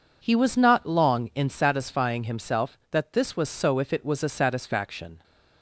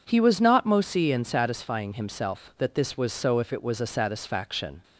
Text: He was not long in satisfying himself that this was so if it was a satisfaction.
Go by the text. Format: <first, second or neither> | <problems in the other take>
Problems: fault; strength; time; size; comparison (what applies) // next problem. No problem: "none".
first | says "mosi" for "long"; at 0.6 s